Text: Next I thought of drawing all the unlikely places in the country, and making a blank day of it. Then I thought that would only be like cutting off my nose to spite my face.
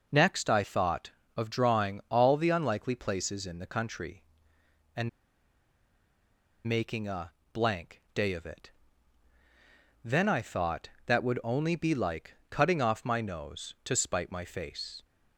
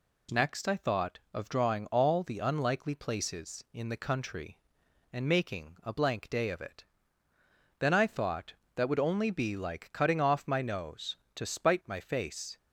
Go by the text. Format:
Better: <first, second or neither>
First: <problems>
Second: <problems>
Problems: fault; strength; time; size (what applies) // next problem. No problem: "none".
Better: second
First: pauses between "and" and "making"; strong; at 5.0 s; 1.5 s long // pauses between "a" and "blank"; slight; at 7.3 s; 0.22 s long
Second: none